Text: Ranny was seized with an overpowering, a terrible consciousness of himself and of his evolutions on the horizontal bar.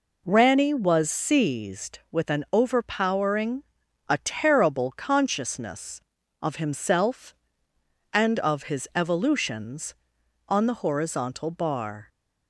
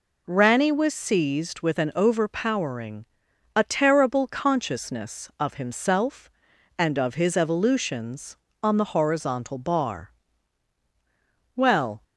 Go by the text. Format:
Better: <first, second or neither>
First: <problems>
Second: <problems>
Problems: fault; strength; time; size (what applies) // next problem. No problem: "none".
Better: first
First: none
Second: goes on to say "Well"; slight; from 11.5 s on; 0.48 s long